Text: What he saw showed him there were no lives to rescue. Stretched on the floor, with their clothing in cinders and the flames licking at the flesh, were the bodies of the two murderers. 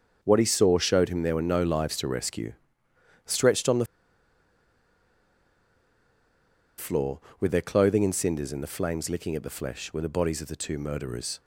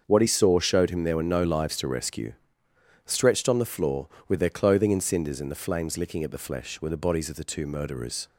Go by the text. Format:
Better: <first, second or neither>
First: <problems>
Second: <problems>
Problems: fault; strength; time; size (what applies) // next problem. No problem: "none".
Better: second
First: starts louder than the rest; until 1.2 s; 6.5 dB // pauses between "the" and "floor"; strong; at 3.8 s; 2.9 s long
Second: starts louder than the rest; until 1.0 s; 6.5 dB